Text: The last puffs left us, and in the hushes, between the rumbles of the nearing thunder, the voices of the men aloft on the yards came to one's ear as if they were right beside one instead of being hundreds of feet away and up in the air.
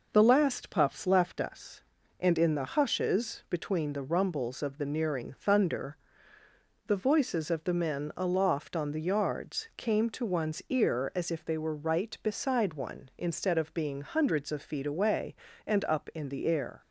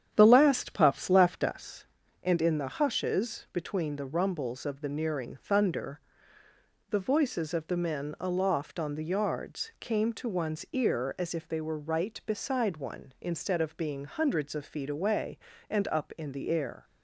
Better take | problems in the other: first | starts louder than the rest; strong; until 2.0 s; 9 dB

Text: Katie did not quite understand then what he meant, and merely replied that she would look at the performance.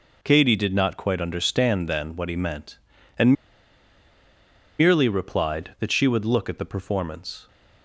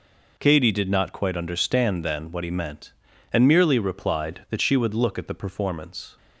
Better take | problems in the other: second | pauses between "and" and "merely"; strong; at 3.3 s; 1.4 s long

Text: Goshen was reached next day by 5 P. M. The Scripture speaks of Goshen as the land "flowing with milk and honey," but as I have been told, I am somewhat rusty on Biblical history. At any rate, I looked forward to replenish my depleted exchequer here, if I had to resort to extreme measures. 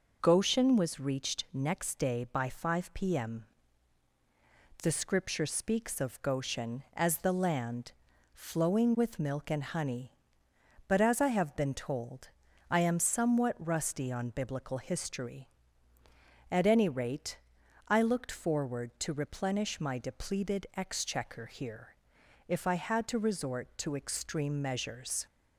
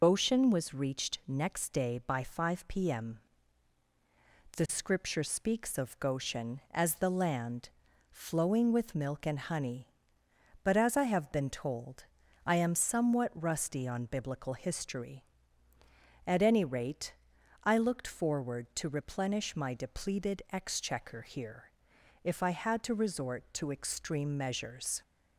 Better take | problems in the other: first | loses the start of "Goshen"; at 0.0 s; 60 ms // pauses between "M" and "The"; strong; at 3.2 s; 1.3 s long; strong in the first // pauses between "land" and "flowing"; at 7.6 s; 0.42 s long; also in the first

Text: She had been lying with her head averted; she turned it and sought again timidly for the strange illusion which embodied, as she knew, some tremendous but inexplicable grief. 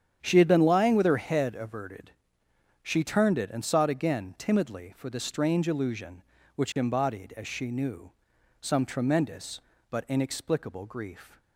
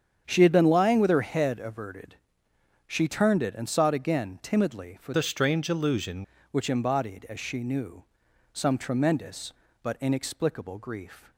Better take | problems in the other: first | starts louder than the rest; strong; until 1.2 s; 8 dB; strong in the first // changes voice from "the" to "illusion"; from 5.1 to 6.2 s; 1.1 s long

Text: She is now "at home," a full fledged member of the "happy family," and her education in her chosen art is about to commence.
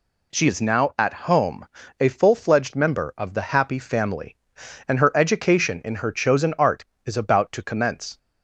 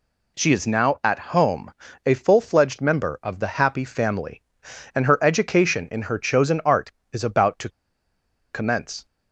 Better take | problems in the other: first | pauses between "to" and "commence"; noticeable; at 7.6 s; 0.83 s long

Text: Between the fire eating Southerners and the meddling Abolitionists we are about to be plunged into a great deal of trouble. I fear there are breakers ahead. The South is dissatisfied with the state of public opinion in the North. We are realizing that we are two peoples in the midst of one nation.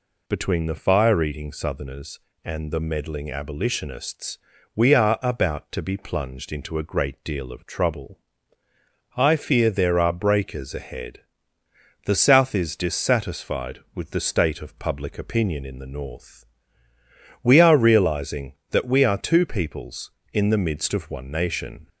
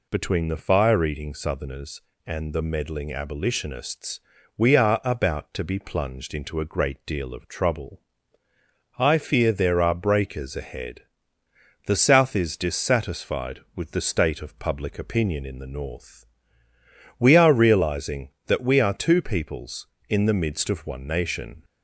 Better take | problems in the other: neither | pauses between "Abolitionists" and "we"; the same in both

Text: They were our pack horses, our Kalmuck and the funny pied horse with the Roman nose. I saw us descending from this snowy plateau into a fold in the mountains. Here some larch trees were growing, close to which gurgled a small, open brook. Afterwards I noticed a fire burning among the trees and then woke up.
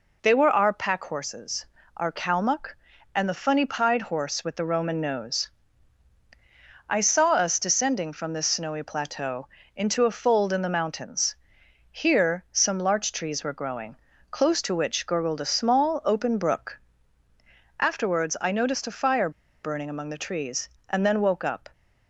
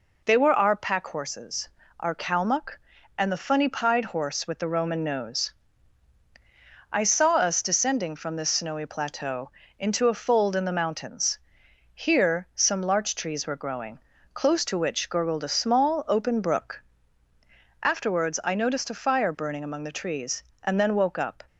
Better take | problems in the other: second | pauses between "plateau" and "into"; slight; at 9.4 s; 0.30 s long; slight in the second // pauses between "fire" and "burning"; slight; at 19.2 s; 0.33 s long

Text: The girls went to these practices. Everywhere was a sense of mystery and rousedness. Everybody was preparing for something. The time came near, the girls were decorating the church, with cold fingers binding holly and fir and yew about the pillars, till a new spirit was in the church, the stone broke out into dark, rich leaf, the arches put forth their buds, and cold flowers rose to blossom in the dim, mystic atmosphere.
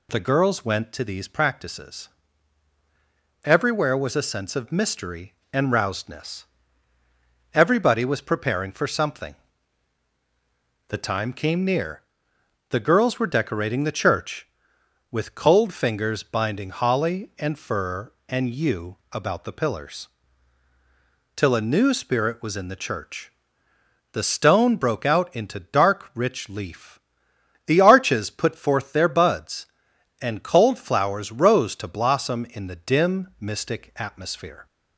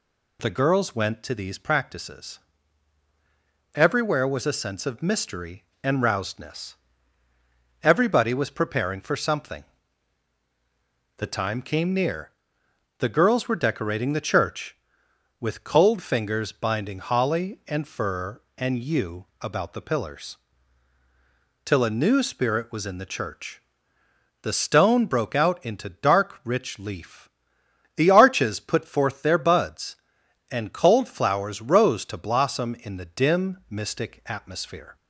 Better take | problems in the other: neither | pauses between "yew" and "about"; slight; the same in both

